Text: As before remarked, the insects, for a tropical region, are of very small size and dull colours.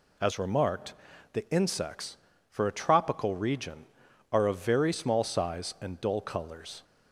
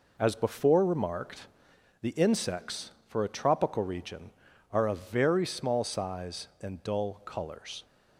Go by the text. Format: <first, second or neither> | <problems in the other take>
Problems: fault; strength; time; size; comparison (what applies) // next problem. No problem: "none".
second | skips "before"; at 0.3 s